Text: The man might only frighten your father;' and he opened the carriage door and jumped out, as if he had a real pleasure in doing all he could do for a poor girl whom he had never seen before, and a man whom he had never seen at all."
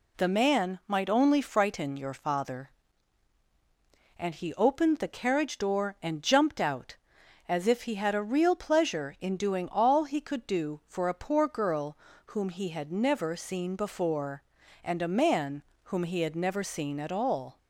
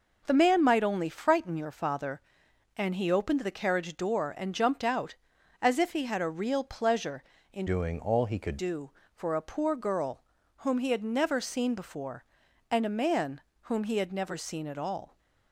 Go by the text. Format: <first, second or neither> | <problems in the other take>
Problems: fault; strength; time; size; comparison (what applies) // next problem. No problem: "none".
first | changes voice from "doing" to "could"; from 7.6 to 8.5 s; 0.9 s long // pauses between "girl" and "whom"; slight; at 10.2 s; 0.34 s long; slight in the first // pauses between "man" and "whom"; slight; at 13.4 s; 0.22 s long; slight in the first